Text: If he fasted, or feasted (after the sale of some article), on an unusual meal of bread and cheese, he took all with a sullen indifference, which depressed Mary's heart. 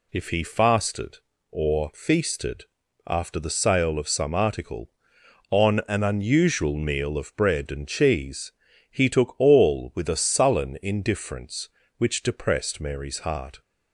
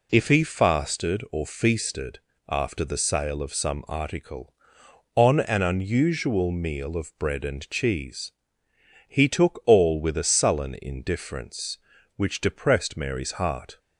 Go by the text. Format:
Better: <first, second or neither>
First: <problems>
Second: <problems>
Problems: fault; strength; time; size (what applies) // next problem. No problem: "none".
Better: neither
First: none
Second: none